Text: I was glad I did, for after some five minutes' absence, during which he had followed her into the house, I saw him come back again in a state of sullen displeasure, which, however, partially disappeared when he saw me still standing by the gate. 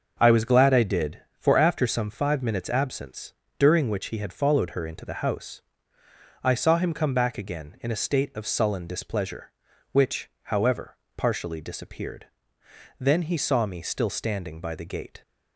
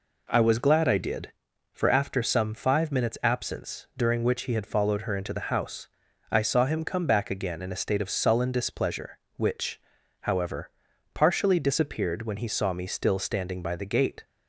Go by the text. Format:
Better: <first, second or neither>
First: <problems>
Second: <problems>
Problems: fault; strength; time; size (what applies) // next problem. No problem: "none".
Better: second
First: starts louder than the rest; until 1.2 s; 6 dB // says "then" for "when"; at 12.9 s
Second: none